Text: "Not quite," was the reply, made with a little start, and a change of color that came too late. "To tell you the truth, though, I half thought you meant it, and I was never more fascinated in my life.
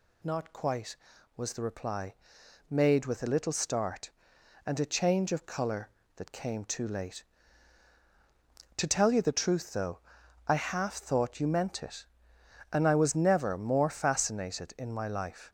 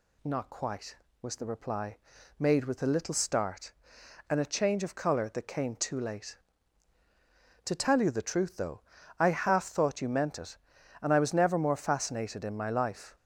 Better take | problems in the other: neither | none

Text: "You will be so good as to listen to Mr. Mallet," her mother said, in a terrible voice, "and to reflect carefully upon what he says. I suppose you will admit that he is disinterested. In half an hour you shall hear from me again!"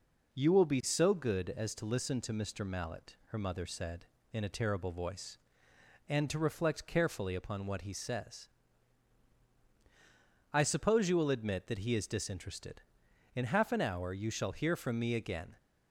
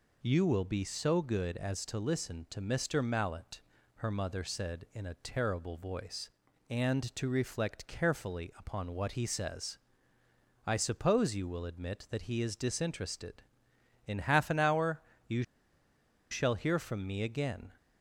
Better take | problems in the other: first | pauses between "hour" and "you"; slight; at 15.0 s; 0.28 s long // pauses between "you" and "shall"; noticeable; at 15.4 s; 0.86 s long

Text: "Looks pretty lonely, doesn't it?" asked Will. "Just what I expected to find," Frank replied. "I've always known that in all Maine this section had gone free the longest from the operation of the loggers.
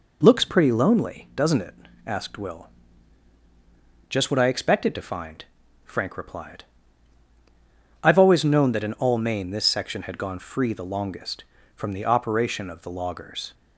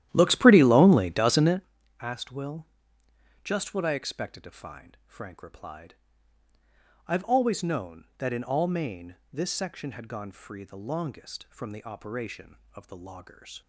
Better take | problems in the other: first | starts louder than the rest; strong; until 1.7 s; 12.5 dB

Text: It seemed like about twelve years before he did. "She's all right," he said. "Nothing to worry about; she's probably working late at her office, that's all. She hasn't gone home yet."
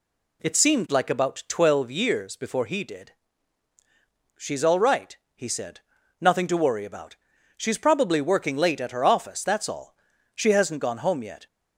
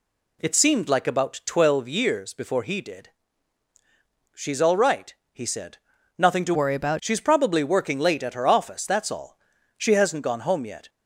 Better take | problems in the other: first | changes voice from "worry" to "about"; from 6.5 to 6.9 s; 0.4 s long

